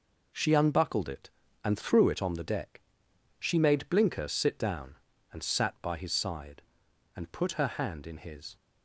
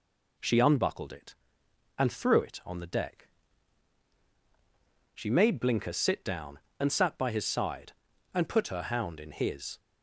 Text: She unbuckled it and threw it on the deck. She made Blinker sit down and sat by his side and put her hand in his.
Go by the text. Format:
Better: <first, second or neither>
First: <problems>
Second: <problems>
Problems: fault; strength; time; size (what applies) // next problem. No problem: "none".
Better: first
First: none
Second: says "hound" for "hand"; at 8.8 s